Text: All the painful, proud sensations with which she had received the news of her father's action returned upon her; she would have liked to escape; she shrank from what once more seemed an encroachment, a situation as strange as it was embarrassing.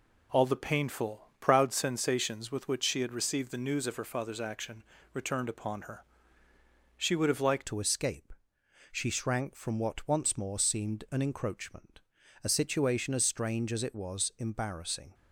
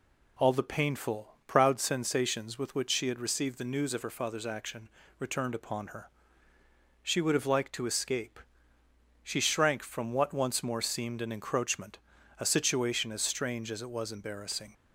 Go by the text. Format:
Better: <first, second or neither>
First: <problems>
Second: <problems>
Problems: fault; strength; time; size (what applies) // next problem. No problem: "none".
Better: second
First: pauses between "action" and "returned"; slight; at 4.8 s; 0.28 s long // changes voice at "to"; from 7.6 s on; 7.5 s long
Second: pauses between "action" and "returned"; slight; at 4.8 s; 0.28 s long